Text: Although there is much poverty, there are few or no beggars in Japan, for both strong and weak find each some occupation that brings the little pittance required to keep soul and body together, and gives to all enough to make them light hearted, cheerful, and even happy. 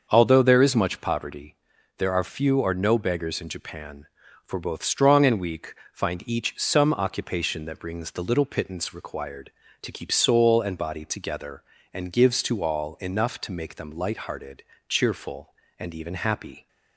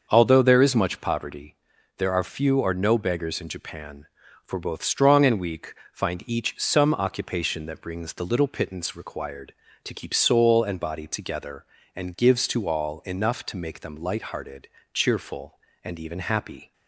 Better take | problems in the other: neither | starts louder than the rest; the same in both // pauses between "weak" and "find"; slight; the same in both

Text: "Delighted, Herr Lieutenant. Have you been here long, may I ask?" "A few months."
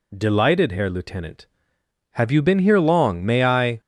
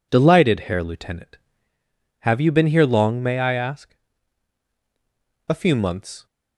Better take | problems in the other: second | stops before "ask A few months"; at 3.8 s

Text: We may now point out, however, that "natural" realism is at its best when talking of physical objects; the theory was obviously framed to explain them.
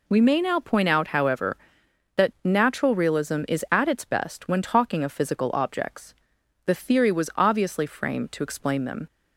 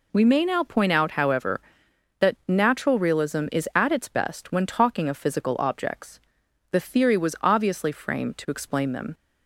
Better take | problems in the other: neither | none

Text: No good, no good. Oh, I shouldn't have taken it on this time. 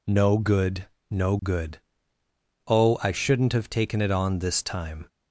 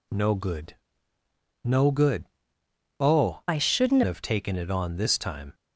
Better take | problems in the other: first | changes voice from "I" to "shouldn't"; from 3.4 to 4.0 s; 0.6 s long

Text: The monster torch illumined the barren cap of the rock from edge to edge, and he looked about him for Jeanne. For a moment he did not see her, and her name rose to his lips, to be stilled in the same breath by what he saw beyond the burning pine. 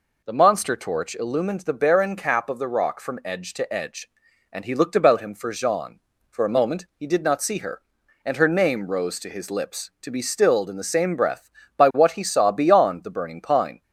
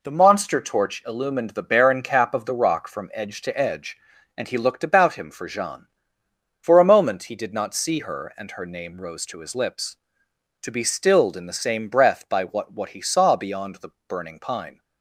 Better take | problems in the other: first | says "what" twice; at 12.7 s // pauses between "the" and "burning"; slight; at 13.9 s; 0.16 s long

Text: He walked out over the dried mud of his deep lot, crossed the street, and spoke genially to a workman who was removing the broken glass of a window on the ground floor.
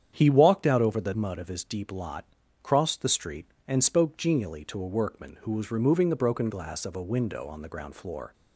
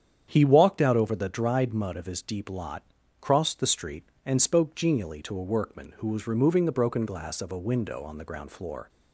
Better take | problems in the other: second | starts louder than the rest; strong; until 1.1 s; 8.5 dB; strong in the second // skips "dried"; at 1.1 s

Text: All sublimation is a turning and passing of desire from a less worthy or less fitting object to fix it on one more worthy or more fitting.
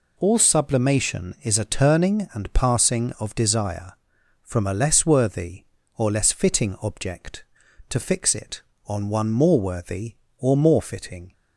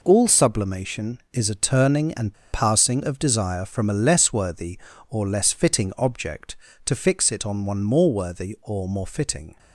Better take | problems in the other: first | pauses between "and" and "passing"; slight; at 2.3 s; 0.18 s long

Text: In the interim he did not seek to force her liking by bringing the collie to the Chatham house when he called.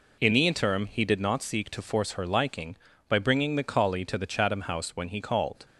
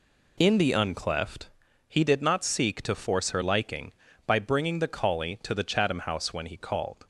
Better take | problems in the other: first | says "uncleft" for "interim"; at 0.7 s

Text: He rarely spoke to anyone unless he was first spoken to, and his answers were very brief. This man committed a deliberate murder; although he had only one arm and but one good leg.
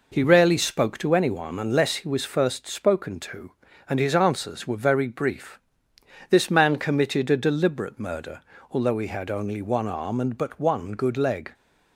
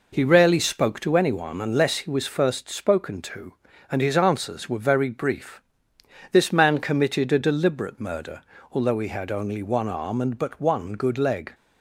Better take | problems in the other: neither | none

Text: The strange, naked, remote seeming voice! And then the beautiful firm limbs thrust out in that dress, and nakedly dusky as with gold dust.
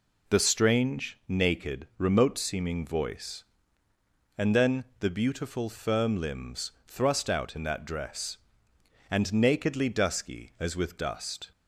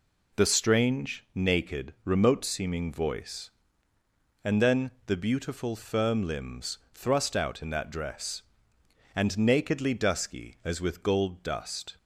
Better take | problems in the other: second | pauses between "then" and "the"; slight; at 4.8 s; 0.16 s long; slight in the second // pauses between "limbs" and "thrust"; slight; at 6.7 s; 0.16 s long; slight in the second // skips "gold"; at 10.9 s

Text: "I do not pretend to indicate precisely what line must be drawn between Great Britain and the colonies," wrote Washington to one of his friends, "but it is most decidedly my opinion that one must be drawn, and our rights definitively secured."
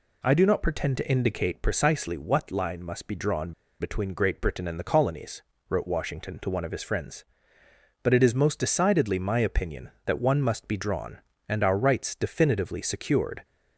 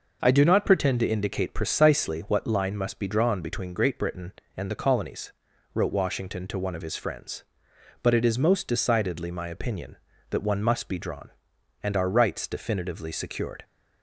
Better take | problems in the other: second | pauses between "drawn" and "between"; slight; at 3.5 s; 0.28 s long

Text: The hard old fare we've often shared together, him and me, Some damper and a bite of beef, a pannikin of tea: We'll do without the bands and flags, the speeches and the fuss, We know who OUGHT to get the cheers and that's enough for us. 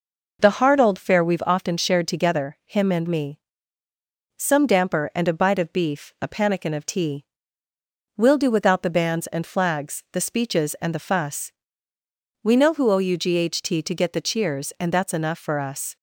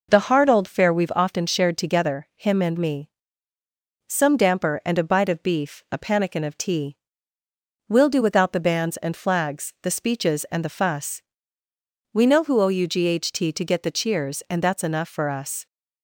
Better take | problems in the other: neither | none

